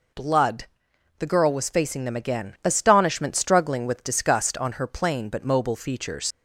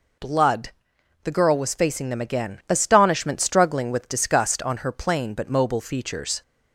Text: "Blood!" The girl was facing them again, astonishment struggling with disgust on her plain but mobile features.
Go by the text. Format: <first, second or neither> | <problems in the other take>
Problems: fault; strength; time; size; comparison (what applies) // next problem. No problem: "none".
second | leaves "features" unfinished; at 6.3 s; 65 ms